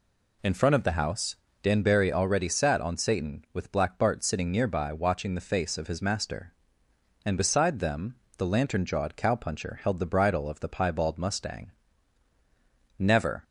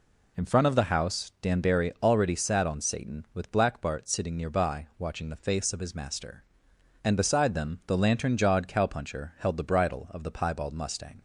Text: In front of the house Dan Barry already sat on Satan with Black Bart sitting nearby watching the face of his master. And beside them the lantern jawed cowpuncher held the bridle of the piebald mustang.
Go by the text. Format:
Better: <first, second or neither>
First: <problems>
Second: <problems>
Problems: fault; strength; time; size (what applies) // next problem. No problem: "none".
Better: second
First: pauses between "house" and "Dan"; slight; at 1.3 s; 0.28 s long // pauses between "them" and "the"; slight; at 8.1 s; 0.22 s long // goes on to say "Never"; slight; from 12.9 s on; 0.46 s long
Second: none